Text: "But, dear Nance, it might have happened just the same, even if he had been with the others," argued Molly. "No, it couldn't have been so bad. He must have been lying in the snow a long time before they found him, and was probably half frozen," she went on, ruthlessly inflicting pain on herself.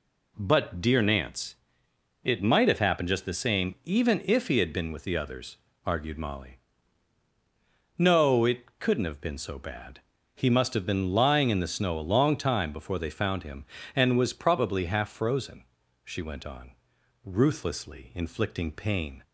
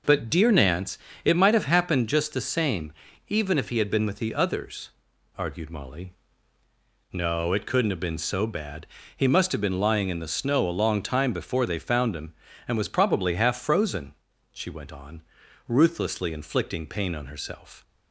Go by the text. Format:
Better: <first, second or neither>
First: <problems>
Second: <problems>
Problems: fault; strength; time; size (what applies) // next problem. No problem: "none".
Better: second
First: stops before "on herself"; at 19.2 s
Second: none